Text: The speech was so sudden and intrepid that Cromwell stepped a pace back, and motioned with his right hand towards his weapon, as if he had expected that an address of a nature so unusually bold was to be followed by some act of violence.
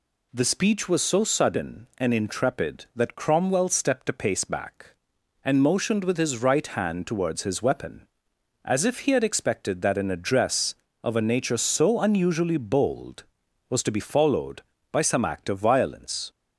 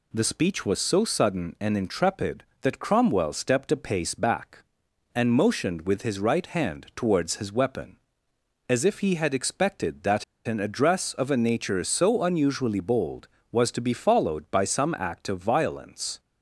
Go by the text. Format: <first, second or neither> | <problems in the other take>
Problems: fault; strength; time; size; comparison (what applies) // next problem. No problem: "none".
first | pauses between "that" and "an"; slight; at 10.2 s; 0.23 s long